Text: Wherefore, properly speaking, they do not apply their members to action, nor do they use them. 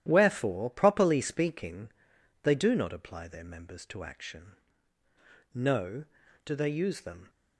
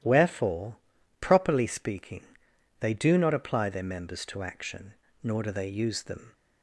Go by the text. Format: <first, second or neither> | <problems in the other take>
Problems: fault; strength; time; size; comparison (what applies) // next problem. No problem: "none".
second | starts louder than the rest; strong; until 1.0 s; 11.5 dB // says "no" for "nor"; at 5.5 s